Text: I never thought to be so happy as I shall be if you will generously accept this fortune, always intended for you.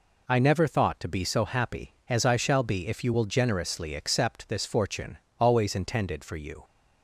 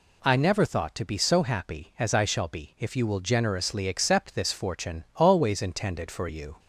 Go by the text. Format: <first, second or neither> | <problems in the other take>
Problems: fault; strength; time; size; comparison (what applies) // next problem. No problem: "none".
neither | none